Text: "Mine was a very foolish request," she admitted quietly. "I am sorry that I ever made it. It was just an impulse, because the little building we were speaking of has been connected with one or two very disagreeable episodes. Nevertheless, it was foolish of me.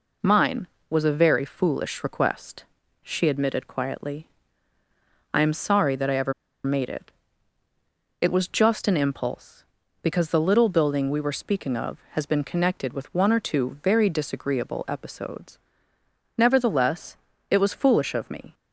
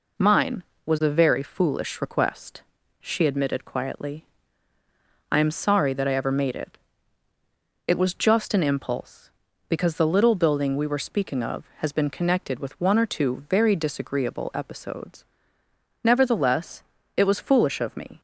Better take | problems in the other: second | pauses between "ever" and "made"; slight; at 6.3 s; 0.32 s long

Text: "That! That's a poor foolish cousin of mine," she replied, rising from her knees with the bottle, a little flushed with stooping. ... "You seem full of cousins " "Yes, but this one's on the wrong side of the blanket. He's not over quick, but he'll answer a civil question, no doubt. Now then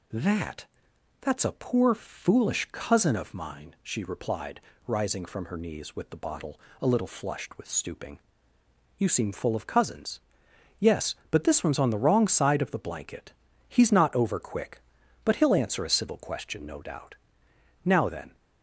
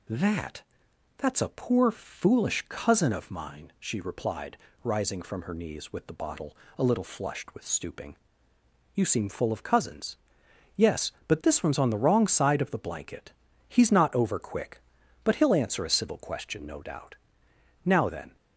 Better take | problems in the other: neither | none

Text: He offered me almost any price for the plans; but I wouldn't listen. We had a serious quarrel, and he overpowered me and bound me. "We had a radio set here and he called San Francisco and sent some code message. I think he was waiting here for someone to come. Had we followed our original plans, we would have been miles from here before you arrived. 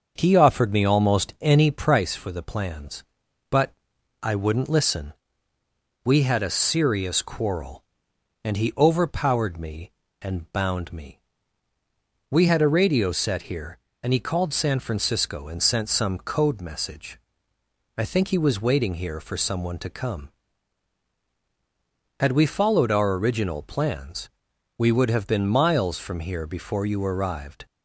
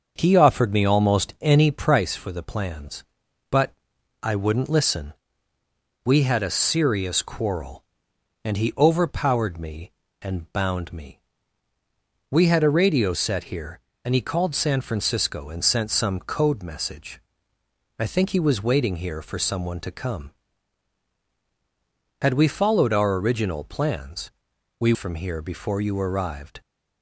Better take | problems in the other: first | starts louder than the rest; until 1.1 s; 6.5 dB; also in the first // pauses between "but" and "I"; noticeable; at 3.7 s; 0.48 s long; noticeable in the first // skips "would have been miles"; at 24.9 s

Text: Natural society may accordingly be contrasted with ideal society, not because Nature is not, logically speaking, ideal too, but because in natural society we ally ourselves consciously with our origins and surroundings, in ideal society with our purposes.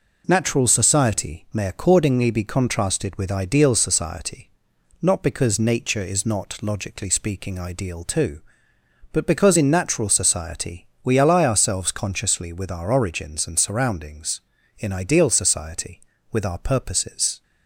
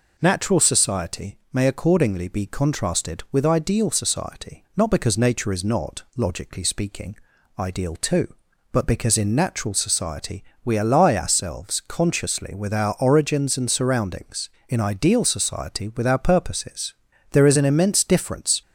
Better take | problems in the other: first | pauses between "society" and "may"; slight; at 1.3 s; 0.16 s long // pauses between "society" and "we"; slight; at 10.4 s; 0.22 s long; slight in the first // goes on to say "There is an immense difference"; noticeable; from 17.3 s on; 1.3 s long

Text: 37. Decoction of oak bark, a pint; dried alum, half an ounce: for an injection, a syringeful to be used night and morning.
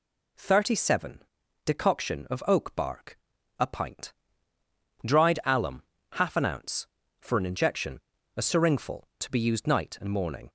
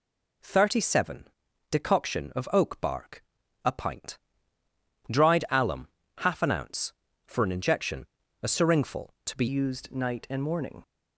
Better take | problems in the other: first | changes voice at "used"; from 9.4 s on; 1.4 s long

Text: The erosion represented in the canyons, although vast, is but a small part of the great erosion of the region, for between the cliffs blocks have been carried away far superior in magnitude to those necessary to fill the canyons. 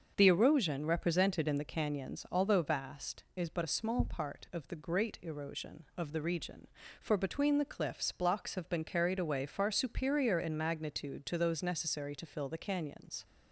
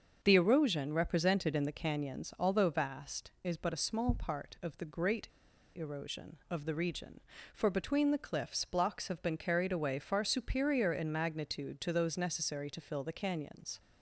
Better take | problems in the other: first | starts louder than the rest; until 1.2 s; 7 dB; also in the first // pauses between "great" and "erosion"; noticeable; at 5.2 s; 0.47 s long

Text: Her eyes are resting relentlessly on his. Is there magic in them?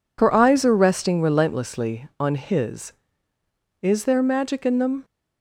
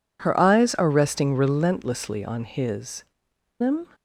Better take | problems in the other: first | skips "Is there magic in"; at 3.3 s

